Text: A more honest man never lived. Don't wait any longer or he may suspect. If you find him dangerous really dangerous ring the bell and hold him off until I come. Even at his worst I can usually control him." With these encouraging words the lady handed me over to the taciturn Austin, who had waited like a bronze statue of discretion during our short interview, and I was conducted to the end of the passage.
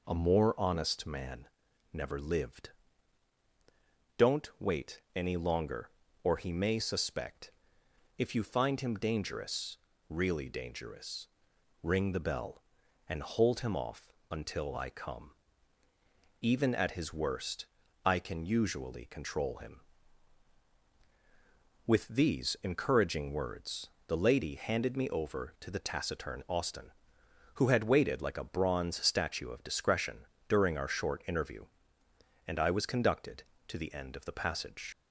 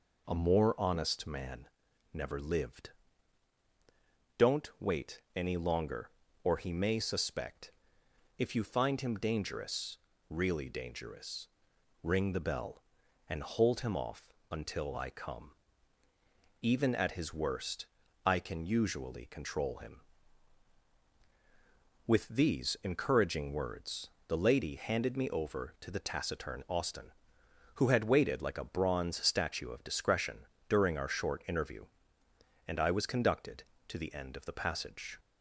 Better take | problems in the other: second | pauses between "man" and "never"; noticeable; at 1.4 s; 0.46 s long; noticeable in the second // pauses between "wait" and "any"; slight; at 4.9 s; 0.16 s long; slight in the second // pauses between "dangerous" and "really"; slight; at 9.7 s; 0.32 s long; slight in the second // pauses between "dangerous" and "ring"; noticeable; at 11.2 s; 0.54 s long; noticeable in the second // pauses between "off" and "until"; slight; at 14.1 s; 0.16 s long; slight in the second // pauses between "worst" and "I"; at 17.6 s; 0.38 s long; also in the second // pauses between "words" and "the"; slight; at 23.8 s; 0.20 s long; slight in the second // pauses between "discretion" and "during"; slight; at 30.2 s; 0.24 s long; slight in the second // leaves "passage" unfinished; at 34.9 s; 60 ms

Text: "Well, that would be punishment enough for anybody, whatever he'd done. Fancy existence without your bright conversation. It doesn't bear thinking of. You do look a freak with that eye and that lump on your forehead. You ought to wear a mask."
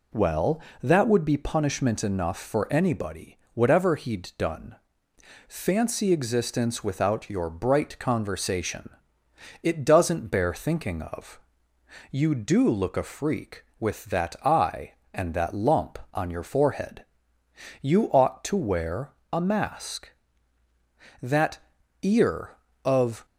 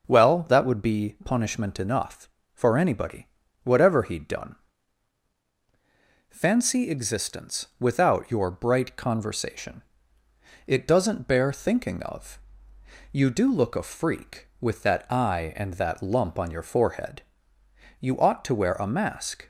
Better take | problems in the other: second | pauses between "wear" and "a"; slight; at 19.1 s; 0.18 s long // goes on to say "That ear of"; strong; from 21.2 s on; 2.0 s long

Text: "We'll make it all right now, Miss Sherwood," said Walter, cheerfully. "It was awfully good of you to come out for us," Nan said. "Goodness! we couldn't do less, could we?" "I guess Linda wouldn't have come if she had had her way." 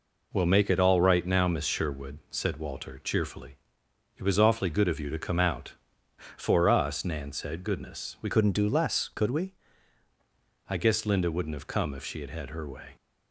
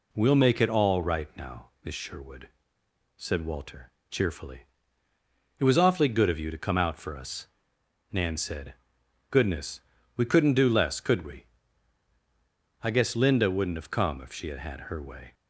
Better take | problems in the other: second | changes voice from "couldn't" to "we"; from 8.2 to 9.5 s; 1.3 s long

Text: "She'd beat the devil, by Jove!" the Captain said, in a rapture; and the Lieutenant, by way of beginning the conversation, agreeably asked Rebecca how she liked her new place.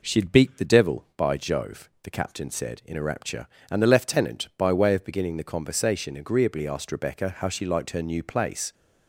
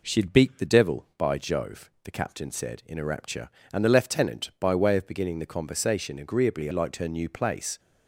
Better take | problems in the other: first | skips "asked Rebecca how she"; at 6.7 s

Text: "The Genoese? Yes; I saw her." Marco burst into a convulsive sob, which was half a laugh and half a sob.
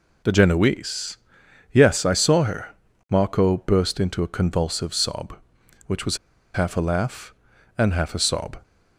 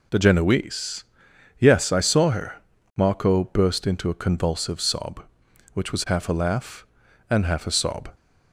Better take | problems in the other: second | pauses between "was" and "half"; at 6.1 s; 0.37 s long

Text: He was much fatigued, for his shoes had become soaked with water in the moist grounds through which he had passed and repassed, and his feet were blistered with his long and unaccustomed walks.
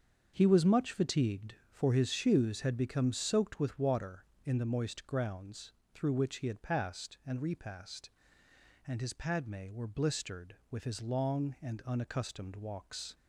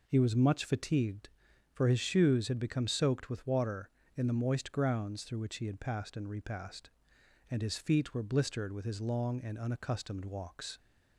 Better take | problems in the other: second | starts louder than the rest; until 1.3 s; 7 dB // pauses between "grounds" and "through"; slight; at 5.7 s; 0.22 s long // says "padme" for "feet"; at 9.1 s

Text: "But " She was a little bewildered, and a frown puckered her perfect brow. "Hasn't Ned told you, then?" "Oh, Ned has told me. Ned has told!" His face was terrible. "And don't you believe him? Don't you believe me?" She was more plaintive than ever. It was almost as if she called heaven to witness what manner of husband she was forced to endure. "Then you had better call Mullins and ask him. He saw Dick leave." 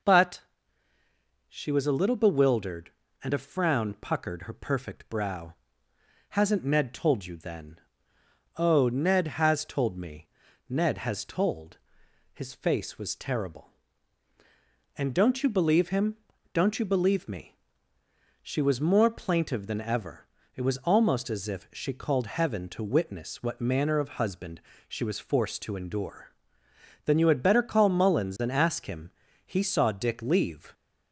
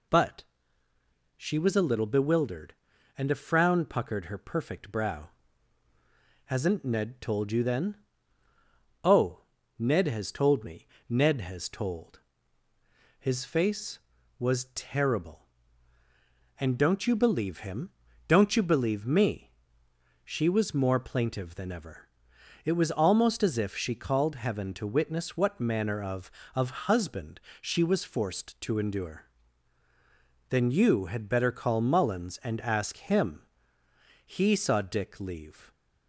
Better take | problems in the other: first | says "of" twice; at 26.5 s // pauses between "husband" and "she"; slight; at 27.4 s; 0.20 s long; slight in the first

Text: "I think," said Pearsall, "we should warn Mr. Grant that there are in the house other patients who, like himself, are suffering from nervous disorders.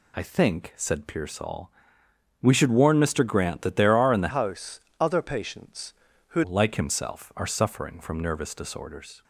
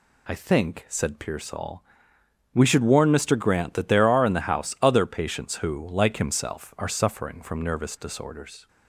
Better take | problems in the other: second | changes voice from "house" to "who"; from 4.3 to 6.4 s; 2.1 s long // pauses between "house" and "other"; slight; at 4.7 s; 0.22 s long

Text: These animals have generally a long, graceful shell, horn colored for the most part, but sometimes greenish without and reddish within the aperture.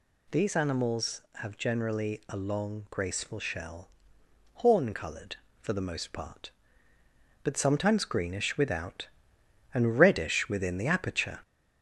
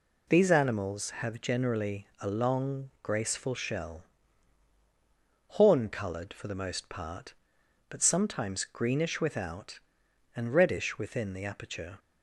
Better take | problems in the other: second | gets louder; slight; throughout; 2.5 dB

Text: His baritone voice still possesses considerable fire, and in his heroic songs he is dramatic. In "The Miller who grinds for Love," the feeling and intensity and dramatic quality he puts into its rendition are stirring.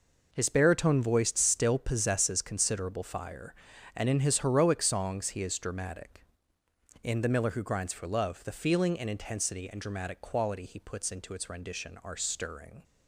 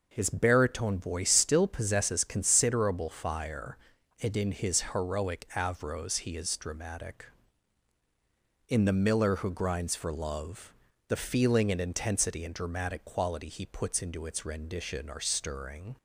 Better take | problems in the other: first | says "avros" for "songs"; at 5.5 s

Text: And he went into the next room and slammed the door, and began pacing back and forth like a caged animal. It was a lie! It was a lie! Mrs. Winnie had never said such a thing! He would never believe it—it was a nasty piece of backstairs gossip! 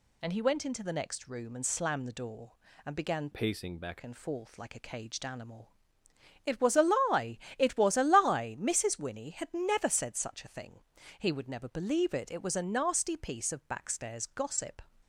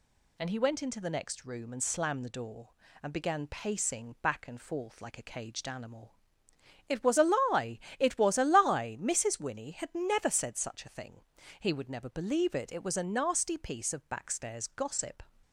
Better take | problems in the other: second | changes voice from "pacing" to "back"; from 3.3 to 3.9 s; 0.6 s long

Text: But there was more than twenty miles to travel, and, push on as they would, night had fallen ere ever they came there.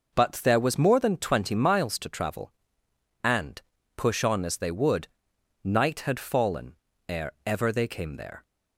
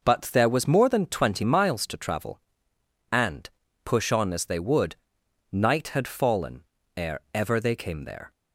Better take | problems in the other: neither | pauses between "fallen" and "ere"; slight; the same in both

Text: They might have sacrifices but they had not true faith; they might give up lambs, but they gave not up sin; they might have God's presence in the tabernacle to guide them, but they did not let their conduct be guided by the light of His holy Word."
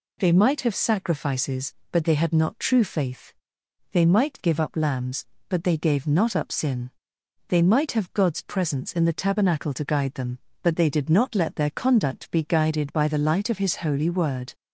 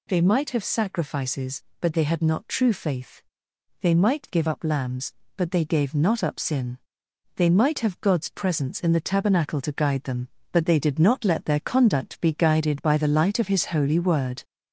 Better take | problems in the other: first | gets louder; slight; throughout; 3 dB

